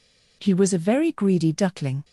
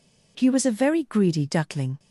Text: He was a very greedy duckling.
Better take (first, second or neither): neither